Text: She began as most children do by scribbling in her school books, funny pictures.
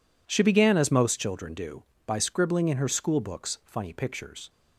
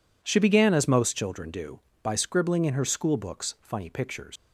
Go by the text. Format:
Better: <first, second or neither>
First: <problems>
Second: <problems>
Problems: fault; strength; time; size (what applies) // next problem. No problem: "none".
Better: first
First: none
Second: leaves "pictures" unfinished; at 4.3 s; 100 ms